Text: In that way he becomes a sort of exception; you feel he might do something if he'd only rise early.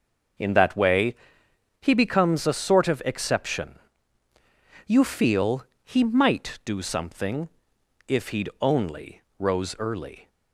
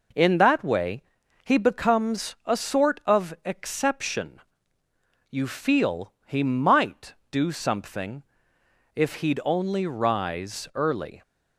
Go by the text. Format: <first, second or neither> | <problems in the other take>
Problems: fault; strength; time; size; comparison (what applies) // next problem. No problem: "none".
second | starts louder than the rest; until 2.0 s; 6 dB // pauses between "way" and "he"; noticeable; at 1.1 s; 0.66 s long; also in the second // pauses between "feel" and "he"; slight; at 5.6 s; 0.20 s long // pauses between "something" and "if"; noticeable; at 7.4 s; 0.62 s long; noticeable in the second // says "rose" for "rise"; at 9.3 s